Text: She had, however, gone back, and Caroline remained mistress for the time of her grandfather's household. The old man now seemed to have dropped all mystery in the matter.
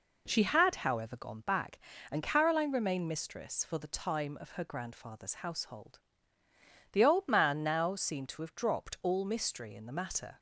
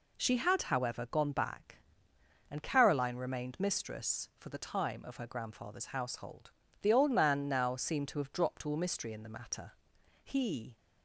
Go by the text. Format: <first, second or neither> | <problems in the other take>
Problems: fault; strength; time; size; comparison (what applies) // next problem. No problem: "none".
first | goes on to say "He"; from 10.2 s on; 0.54 s long